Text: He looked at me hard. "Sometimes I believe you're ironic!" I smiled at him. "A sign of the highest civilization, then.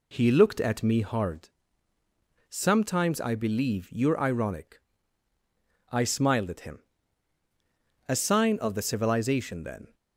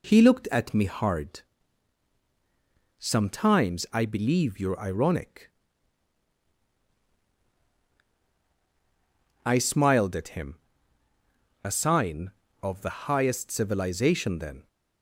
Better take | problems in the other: second | skips "highest"; at 8.8 s

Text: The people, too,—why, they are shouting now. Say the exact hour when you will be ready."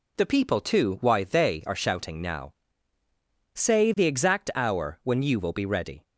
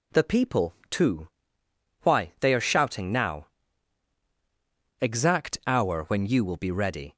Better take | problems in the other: first | skips "Say the"; at 4.2 s

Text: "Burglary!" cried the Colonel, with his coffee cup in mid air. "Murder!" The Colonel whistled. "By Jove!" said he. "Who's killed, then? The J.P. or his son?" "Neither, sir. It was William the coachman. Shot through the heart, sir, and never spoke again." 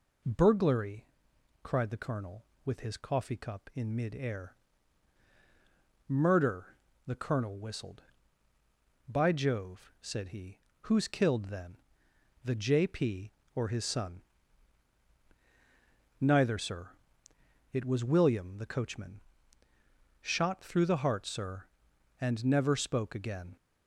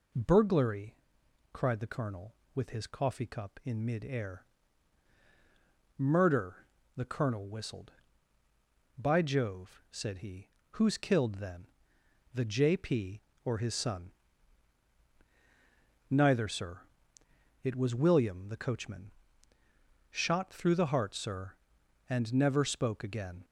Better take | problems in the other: neither | none

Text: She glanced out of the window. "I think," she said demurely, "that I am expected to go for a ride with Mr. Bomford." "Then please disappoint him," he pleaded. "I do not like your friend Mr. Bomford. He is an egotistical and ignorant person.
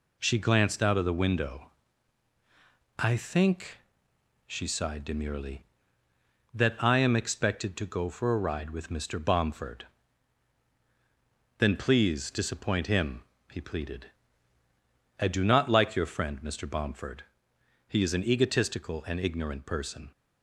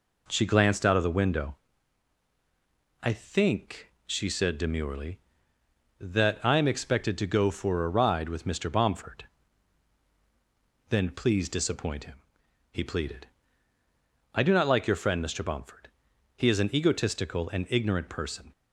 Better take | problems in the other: second | says "sighed" for "said"; at 4.6 s

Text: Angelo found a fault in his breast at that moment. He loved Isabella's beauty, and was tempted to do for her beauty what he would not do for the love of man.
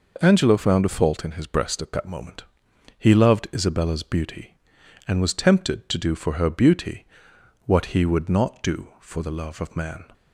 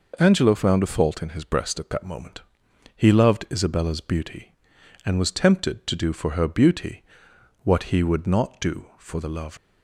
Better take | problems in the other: first | pauses between "beauty" and "what"; noticeable; at 7.0 s; 0.62 s long; noticeable in the first // stops before "of man"; at 9.5 s

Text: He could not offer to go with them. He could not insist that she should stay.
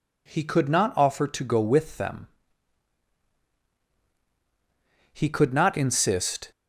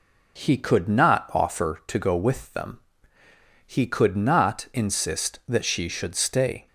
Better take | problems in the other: second | stops before "that she should stay"; at 6.5 s

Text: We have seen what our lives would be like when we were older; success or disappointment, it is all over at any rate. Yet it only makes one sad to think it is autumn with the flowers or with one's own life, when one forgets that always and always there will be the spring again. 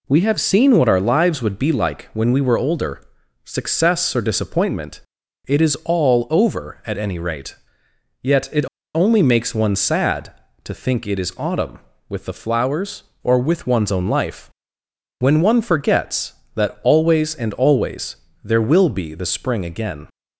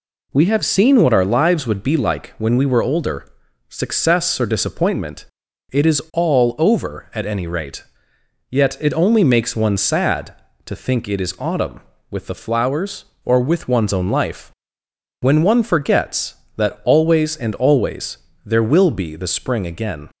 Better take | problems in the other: second | pauses between "it" and "only"; slight; at 8.6 s; 0.28 s long // pauses between "always" and "there"; slight; at 18.1 s; 0.26 s long; slight in the second

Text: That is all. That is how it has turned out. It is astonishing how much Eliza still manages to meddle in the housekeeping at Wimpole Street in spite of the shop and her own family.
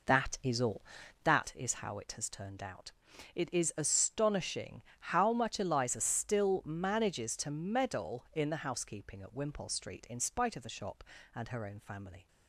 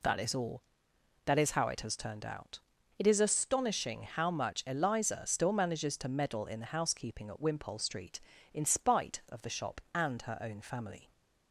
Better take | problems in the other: second | starts louder than the rest; noticeable; until 1.6 s; 4.5 dB // pauses between "astonishing" and "how"; slight; at 4.8 s; 0.18 s long

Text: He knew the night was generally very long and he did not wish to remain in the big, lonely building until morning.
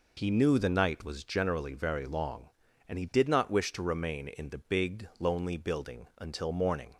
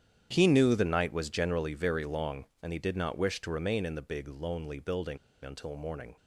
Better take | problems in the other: first | starts louder than the rest; strong; until 1.3 s; 9.5 dB // pauses between "building" and "until"; slight; at 5.1 s; 0.26 s long

